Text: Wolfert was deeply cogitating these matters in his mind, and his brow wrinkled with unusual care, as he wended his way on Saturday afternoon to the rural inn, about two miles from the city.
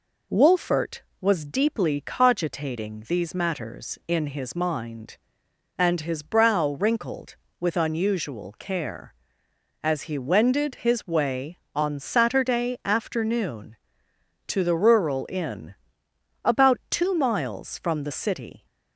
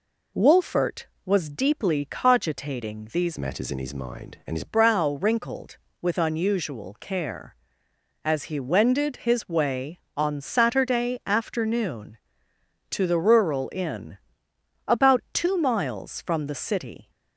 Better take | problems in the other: first | changes voice from "matters" to "his"; from 3.3 to 4.6 s; 1.3 s long

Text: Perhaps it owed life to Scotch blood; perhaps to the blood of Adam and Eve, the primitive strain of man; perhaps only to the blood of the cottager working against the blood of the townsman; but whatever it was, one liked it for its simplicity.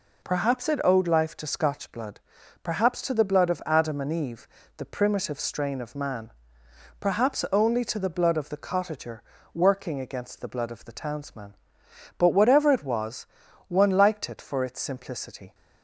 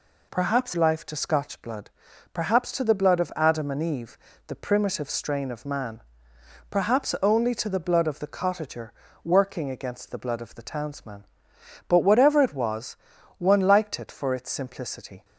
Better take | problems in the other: first | skips "it owed"; at 0.7 s // pauses between "cottager" and "working"; slight; at 8.9 s; 0.32 s long; slight in the first

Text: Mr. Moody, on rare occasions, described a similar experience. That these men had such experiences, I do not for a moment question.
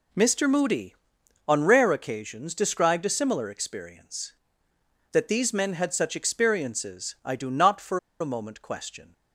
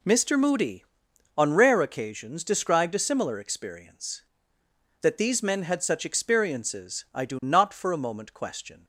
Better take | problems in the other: second | pauses between "for" and "a"; slight; at 7.9 s; 0.22 s long

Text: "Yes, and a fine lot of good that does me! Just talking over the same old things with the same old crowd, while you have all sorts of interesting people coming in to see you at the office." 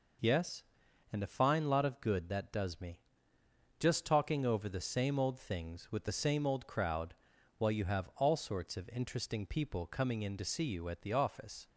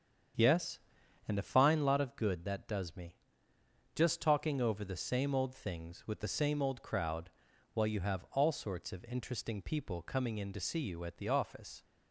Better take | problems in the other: first | starts louder than the rest; strong; until 1.9 s; 7.5 dB

